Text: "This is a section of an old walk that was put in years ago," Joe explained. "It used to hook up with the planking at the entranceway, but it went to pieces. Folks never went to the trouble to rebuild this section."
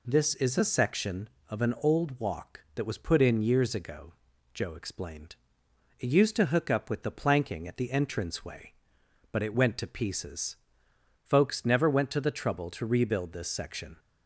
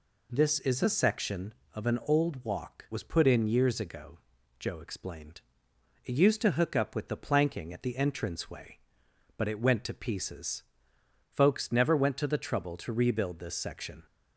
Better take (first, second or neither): first